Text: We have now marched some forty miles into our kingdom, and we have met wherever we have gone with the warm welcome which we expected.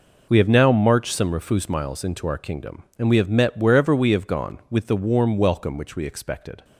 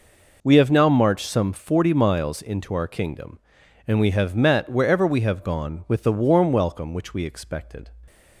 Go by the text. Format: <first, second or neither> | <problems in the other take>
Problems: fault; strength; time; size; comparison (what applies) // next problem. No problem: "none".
second | says "refus" for "forty"; at 1.3 s